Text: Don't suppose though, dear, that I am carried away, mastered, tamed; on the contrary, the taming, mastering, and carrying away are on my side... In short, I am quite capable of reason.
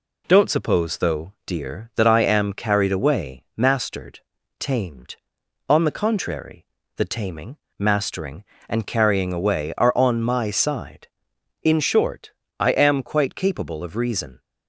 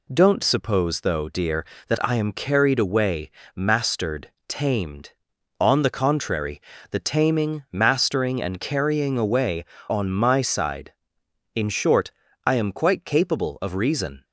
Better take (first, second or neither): first